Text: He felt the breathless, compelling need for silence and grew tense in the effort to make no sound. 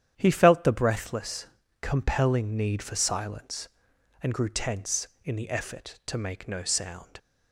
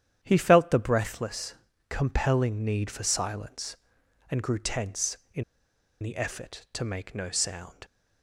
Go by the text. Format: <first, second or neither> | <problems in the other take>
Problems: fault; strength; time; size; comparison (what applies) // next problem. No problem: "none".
first | starts louder than the rest; strong; until 1.2 s; 10 dB; strong in the first // pauses between "in" and "the"; noticeable; at 5.4 s; 0.59 s long